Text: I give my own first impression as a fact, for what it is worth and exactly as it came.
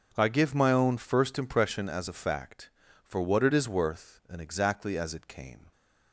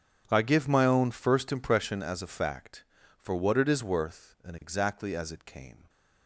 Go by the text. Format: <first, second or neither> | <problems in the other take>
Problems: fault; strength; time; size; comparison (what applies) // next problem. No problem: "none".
first | gets quieter; strong; throughout; 18.5 dB // starts louder than the rest; strong; until 1.2 s; 7.5 dB; also in the first